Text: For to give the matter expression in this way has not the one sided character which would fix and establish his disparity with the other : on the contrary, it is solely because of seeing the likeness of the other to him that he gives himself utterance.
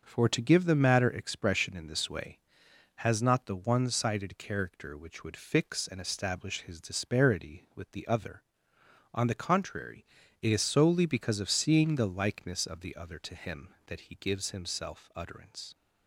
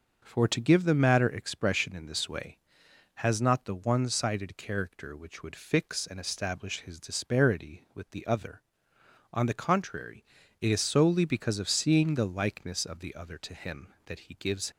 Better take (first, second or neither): first